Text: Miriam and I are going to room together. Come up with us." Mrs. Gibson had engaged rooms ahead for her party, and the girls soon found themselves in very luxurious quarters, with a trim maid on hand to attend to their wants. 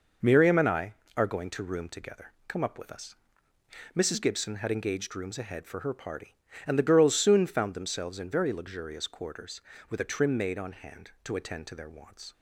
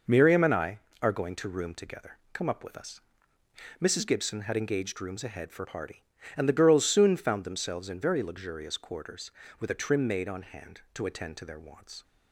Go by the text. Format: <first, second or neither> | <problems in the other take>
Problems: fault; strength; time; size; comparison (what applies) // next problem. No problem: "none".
first | skips "her"; at 5.6 s